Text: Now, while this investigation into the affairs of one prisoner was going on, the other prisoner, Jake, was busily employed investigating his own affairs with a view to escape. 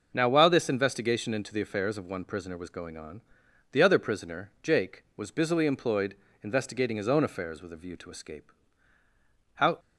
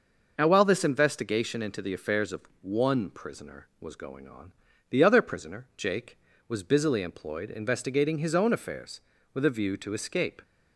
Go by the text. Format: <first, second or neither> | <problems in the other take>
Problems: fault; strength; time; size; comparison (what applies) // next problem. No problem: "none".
second | pauses between "employed" and "investigating"; slight; at 6.1 s; 0.26 s long // goes on to say "How"; slight; from 9.5 s on; 0.24 s long